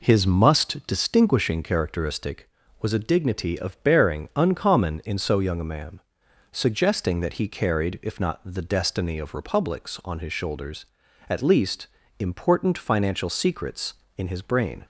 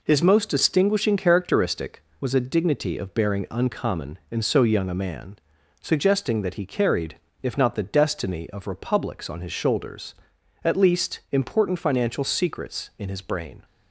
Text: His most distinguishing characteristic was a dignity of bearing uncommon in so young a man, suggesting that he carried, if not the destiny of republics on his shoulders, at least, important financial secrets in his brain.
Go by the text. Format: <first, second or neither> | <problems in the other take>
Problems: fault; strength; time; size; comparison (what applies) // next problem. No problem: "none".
second | says "must" for "most"; at 0.2 s